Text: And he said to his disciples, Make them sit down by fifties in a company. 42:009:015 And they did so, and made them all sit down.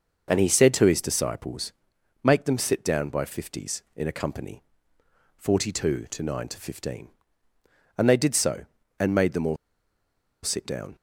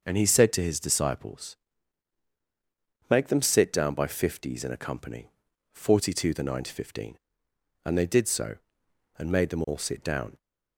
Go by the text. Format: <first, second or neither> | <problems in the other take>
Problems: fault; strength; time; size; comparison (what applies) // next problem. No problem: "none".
second | pauses between "all" and "sit"; noticeable; at 9.5 s; 0.87 s long